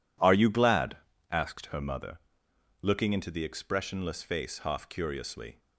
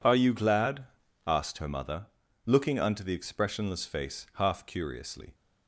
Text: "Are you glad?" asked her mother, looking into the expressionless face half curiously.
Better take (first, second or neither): first